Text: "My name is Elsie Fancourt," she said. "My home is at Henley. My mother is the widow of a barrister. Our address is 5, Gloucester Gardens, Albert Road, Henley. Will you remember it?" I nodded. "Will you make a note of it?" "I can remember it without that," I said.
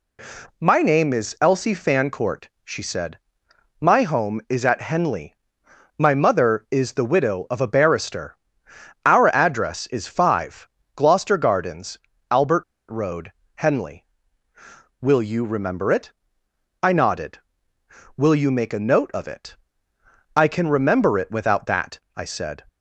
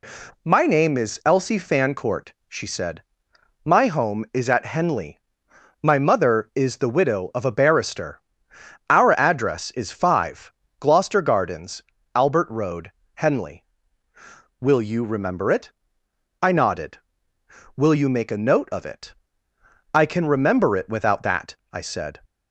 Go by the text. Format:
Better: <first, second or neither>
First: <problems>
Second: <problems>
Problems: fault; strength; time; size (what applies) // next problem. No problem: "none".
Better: second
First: pauses between "Albert" and "Road"; slight; at 12.6 s; 0.27 s long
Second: none